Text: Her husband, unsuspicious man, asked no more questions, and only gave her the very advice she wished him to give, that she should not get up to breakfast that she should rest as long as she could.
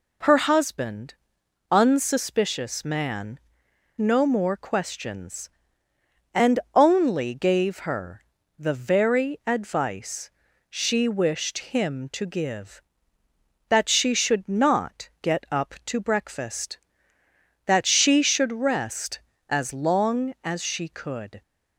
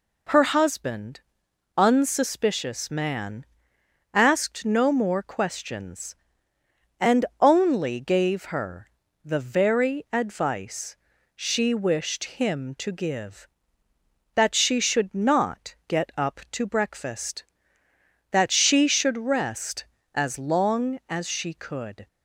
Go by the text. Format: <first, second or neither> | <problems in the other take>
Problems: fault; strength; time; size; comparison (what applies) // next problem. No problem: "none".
second | skips "asked"; at 3.6 s // pauses between "and" and "only"; slight; at 6.5 s; 0.16 s long; slight in the second // pauses between "her" and "the"; slight; at 8.2 s; 0.34 s long; slight in the second // pauses between "advice" and "she"; slight; at 10.3 s; 0.36 s long; slight in the second